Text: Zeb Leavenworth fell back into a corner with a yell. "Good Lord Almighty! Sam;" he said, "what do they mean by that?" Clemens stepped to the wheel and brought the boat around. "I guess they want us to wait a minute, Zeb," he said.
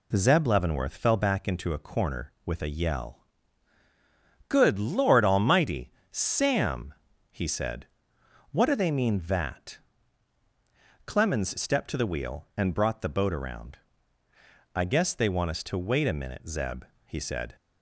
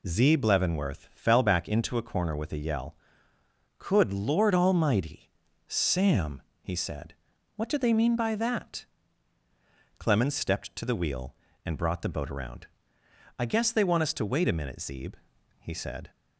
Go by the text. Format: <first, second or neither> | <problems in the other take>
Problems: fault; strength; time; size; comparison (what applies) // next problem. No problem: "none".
second | skips "by"; at 9.2 s